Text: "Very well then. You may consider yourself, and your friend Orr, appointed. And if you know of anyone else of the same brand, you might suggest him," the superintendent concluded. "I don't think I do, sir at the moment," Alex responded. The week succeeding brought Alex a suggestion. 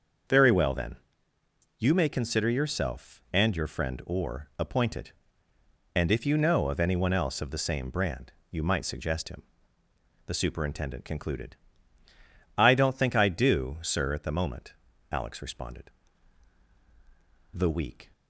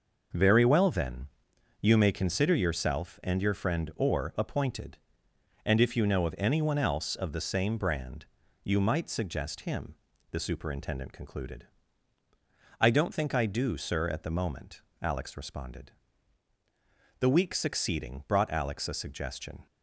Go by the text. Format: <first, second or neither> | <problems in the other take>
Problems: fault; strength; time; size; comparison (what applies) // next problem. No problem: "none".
second | starts louder than the rest; until 2.1 s; 6.5 dB // stops before "succeeding brought Alex a suggestion"; at 18.1 s